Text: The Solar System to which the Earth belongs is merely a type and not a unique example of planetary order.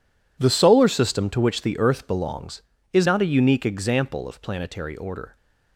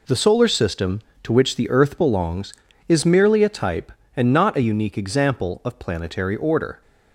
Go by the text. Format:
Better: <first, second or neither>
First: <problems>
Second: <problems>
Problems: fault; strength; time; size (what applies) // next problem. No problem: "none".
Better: second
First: skips "merely a type and"; at 3.0 s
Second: none